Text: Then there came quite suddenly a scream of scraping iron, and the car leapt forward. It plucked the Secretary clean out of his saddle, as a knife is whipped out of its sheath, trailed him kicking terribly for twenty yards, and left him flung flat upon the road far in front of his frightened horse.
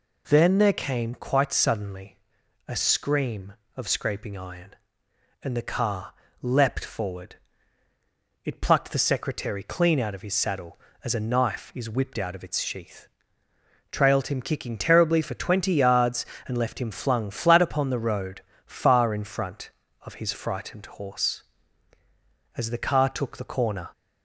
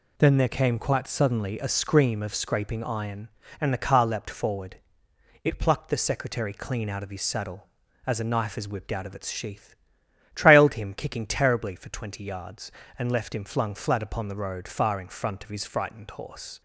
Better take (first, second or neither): second